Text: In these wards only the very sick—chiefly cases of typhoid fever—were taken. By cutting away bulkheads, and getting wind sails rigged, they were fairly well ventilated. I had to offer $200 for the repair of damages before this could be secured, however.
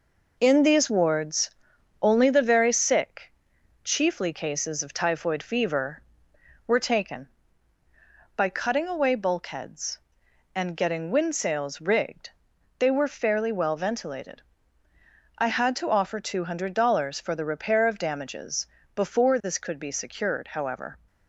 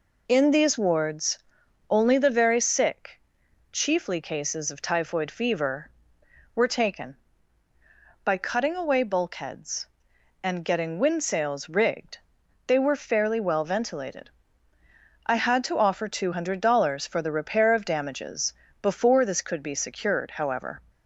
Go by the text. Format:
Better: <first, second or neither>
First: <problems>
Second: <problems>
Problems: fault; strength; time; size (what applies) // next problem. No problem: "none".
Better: second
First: gets quieter; noticeable; throughout; 5 dB // pauses between "wards" and "only"; noticeable; at 1.4 s; 0.50 s long // pauses between "damages" and "before"; slight; at 18.6 s; 0.26 s long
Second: pauses between "wards" and "only"; noticeable; at 1.3 s; 0.50 s long // pauses between "damages" and "before"; slight; at 18.5 s; 0.26 s long